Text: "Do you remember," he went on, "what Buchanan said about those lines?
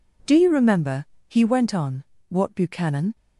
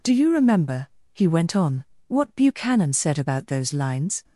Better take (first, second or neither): second